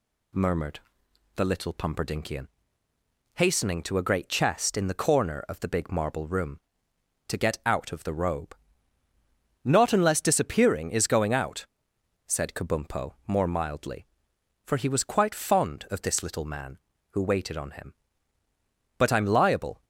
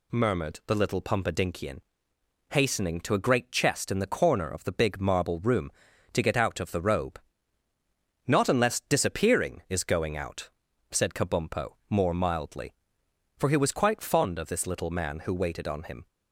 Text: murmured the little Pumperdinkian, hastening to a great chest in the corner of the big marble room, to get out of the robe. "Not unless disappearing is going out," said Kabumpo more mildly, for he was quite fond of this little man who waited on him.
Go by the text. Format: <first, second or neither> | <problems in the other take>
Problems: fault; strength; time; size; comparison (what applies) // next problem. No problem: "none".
second | pauses between "murmured" and "the"; noticeable; at 0.7 s; 0.56 s long // goes on to say "But I'm liable"; noticeable; from 18.9 s on; 0.86 s long